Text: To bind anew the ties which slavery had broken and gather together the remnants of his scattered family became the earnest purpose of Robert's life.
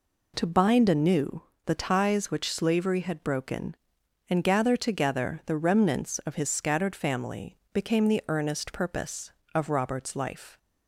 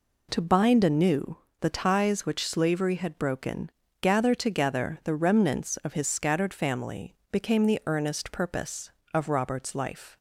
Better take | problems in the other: first | pauses between "anew" and "the"; slight; at 1.3 s; 0.22 s long; slight in the first // skips "and"; at 3.8 s // pauses between "family" and "became"; slight; at 7.1 s; 0.16 s long; slight in the first

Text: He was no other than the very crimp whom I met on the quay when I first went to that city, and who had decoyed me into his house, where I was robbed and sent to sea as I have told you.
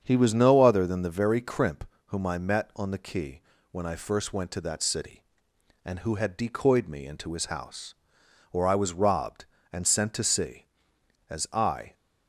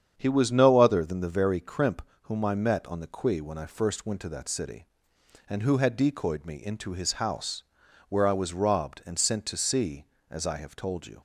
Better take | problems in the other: second | starts louder than the rest; strong; until 1.0 s; 7.5 dB; strong in the second // pauses between "crimp" and "whom"; slight; at 1.8 s; 0.24 s long; slight in the second // pauses between "quay" and "when"; slight; at 3.4 s; 0.30 s long // stops before "have told you"; at 11.9 s

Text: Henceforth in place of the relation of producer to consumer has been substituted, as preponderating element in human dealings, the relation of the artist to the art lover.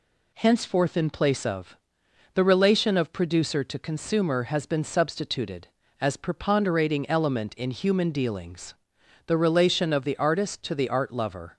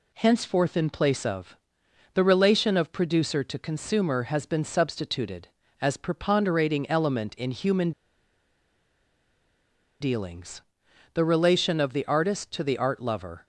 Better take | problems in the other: first | pauses between "of" and "the"; noticeable; at 1.5 s; 0.56 s long; noticeable in the first // pauses between "human" and "dealings"; strong; at 7.9 s; 2.1 s long

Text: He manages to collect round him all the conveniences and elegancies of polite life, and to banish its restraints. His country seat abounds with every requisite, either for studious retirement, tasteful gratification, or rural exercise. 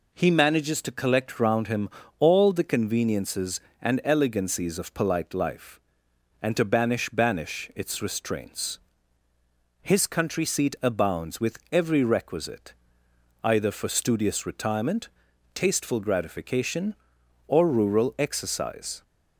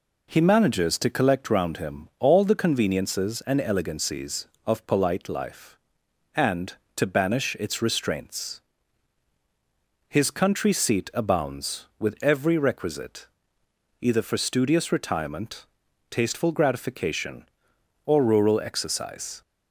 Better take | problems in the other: second | pauses between "him" and "all"; slight; at 1.8 s; 0.30 s long // says "banish" twice; at 7.0 s

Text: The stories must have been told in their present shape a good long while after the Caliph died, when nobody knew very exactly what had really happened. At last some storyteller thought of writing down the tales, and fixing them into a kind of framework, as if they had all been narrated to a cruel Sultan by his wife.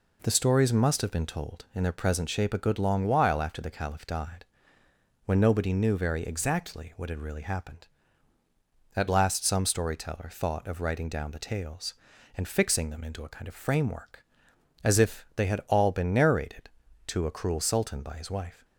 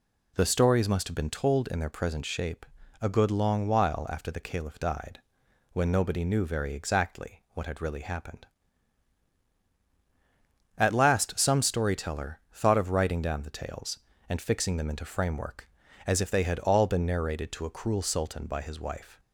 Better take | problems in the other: first | pauses between "shape" and "a"; slight; at 2.6 s; 0.36 s long // skips "a kind of"; at 15.0 s

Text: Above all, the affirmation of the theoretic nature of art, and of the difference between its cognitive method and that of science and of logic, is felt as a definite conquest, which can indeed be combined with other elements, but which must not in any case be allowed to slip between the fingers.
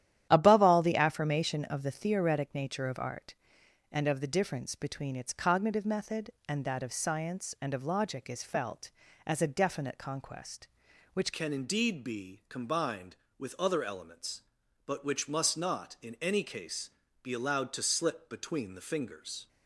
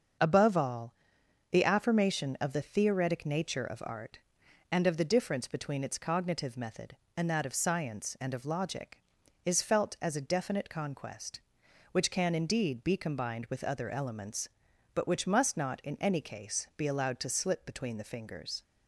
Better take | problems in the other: second | starts louder than the rest; strong; until 1.3 s; 11.5 dB; also in the second // changes voice at "can"; from 11.3 s on; 8.1 s long // pauses between "case" and "be"; slight; at 16.8 s; 0.34 s long

